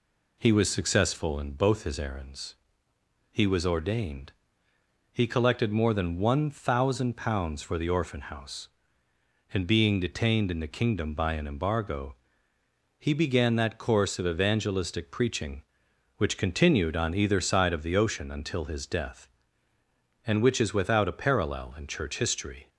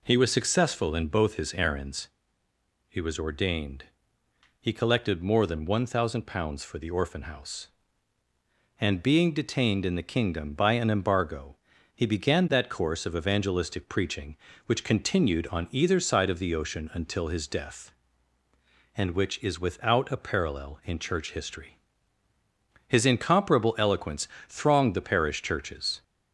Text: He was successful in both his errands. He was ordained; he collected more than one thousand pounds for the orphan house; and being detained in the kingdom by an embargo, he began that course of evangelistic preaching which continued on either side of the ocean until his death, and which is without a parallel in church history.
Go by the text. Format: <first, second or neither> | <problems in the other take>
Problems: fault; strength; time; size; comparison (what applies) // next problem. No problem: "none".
first | goes on to say "His incomparable eloquence thronged the parish churches"; strong; from 22.8 s on; 3.1 s long